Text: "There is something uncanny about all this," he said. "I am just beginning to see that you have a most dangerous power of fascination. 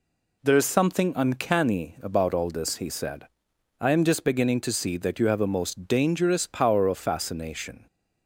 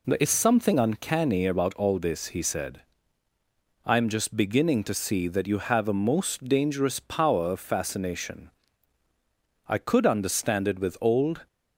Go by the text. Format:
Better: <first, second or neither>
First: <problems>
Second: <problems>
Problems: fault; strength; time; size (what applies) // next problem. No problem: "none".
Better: first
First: none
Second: goes on to say "I could understand it with old"; strong; from 9.6 s on; 1.8 s long